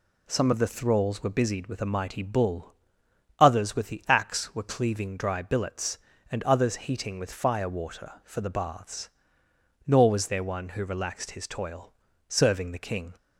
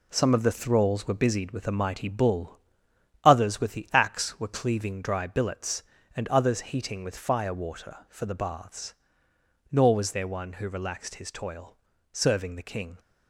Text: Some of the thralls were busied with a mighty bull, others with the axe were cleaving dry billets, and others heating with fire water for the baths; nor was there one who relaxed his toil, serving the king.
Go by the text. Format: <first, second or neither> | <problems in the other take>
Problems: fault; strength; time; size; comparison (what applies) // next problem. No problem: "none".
first | gets quieter; throughout; 6.5 dB